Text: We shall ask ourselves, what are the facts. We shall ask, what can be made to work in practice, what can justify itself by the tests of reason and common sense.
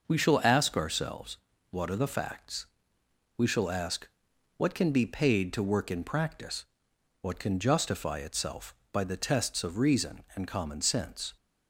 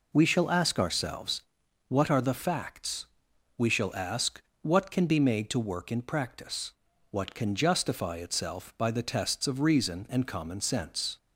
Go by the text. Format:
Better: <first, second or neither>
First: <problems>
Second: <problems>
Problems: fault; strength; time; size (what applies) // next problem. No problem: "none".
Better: second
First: starts louder than the rest; noticeable; until 1.1 s; 6 dB // says "paid" for "made"; at 5.0 s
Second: none